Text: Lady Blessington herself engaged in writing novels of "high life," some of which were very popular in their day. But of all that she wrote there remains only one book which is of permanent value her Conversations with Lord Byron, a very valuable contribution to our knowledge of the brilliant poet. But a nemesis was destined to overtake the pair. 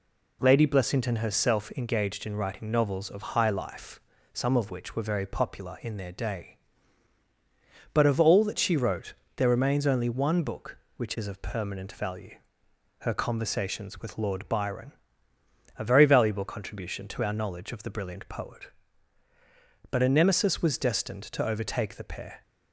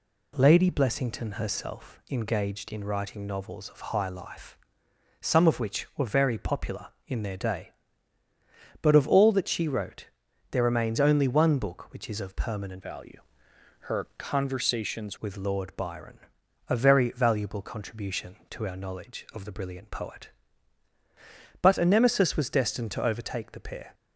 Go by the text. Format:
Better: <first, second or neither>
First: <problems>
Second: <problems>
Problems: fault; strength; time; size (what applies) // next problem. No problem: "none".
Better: first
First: pauses between "wrote" and "there"; slight; at 9.1 s; 0.20 s long // pauses between "value" and "her"; noticeable; at 12.3 s; 0.68 s long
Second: pauses between "wrote" and "there"; at 10.0 s; 0.42 s long // changes voice from "value" to "Conversations"; from 12.8 to 15.1 s; 2.3 s long // pauses between "value" and "her"; noticeable; at 13.1 s; 0.68 s long